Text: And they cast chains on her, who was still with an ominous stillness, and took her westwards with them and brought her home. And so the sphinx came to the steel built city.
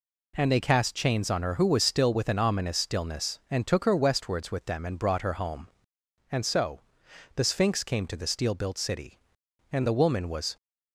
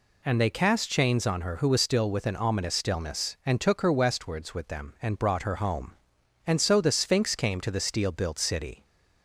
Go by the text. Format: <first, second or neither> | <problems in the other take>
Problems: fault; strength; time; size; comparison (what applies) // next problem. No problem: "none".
second | pauses between "so" and "the"; noticeable; at 6.8 s; 0.54 s long // goes on to say "And the woman was"; noticeable; from 9.7 s on; 0.84 s long